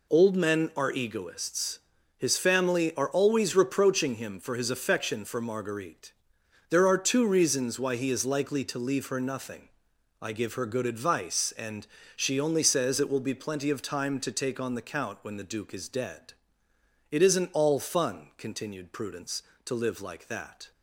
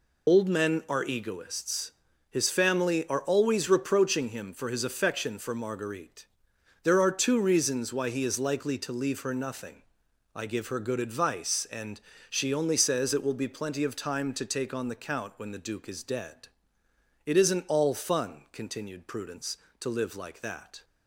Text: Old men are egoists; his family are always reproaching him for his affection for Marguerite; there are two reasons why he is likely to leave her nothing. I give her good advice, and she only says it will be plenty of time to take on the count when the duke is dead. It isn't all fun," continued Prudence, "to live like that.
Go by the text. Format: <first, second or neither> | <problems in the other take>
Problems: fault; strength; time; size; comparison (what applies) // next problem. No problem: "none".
first | loses the start of "Old"; at 0.2 s; 45 ms // pauses between "and" and "she"; slight; at 11.9 s; 0.32 s long; slight in the first